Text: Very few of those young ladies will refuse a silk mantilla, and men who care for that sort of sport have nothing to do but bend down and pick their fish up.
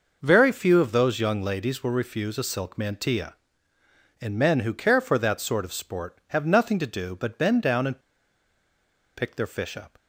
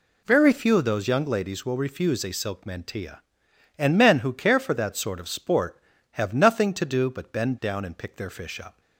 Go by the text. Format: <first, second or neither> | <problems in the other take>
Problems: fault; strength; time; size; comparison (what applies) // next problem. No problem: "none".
second | pauses between "and" and "pick"; at 8.0 s; 1.1 s long